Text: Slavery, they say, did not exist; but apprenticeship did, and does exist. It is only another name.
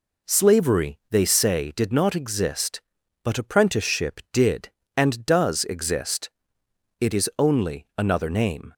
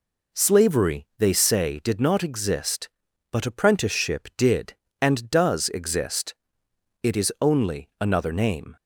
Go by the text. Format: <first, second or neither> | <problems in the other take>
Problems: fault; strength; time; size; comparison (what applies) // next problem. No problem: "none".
neither | none